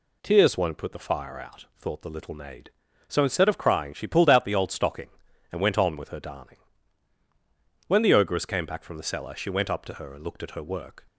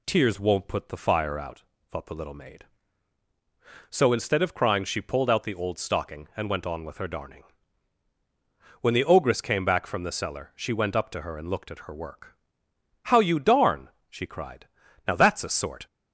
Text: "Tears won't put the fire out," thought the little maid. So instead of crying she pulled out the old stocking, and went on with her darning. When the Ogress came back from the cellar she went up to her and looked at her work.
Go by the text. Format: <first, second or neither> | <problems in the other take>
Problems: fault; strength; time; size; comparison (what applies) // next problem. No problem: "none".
first | goes on to say "How you darn she cried Now that's a sort"; strong; from 13.0 s on; 2.8 s long